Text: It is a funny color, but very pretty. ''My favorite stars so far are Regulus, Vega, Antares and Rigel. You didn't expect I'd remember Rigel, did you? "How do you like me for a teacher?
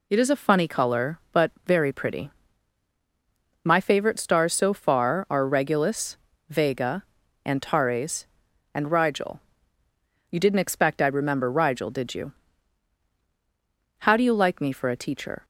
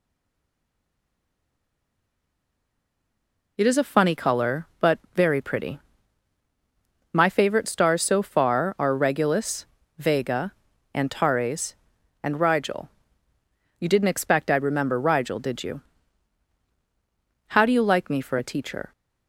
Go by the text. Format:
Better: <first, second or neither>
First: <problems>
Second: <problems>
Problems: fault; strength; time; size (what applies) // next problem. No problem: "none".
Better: first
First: none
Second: stays silent before the first word; strong; until 3.5 s; 3.5 s long // pauses between "but" and "very"; slight; at 4.9 s; 0.16 s long